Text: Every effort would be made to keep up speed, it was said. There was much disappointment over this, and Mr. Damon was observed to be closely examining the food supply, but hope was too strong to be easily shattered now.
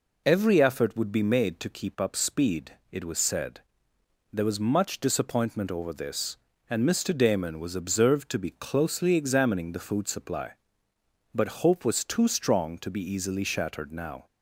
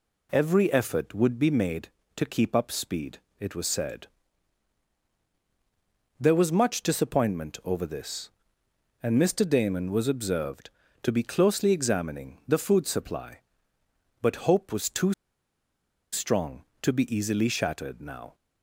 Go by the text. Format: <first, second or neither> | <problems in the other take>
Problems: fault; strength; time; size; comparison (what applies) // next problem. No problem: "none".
first | pauses between "too" and "strong"; at 15.1 s; 1.0 s long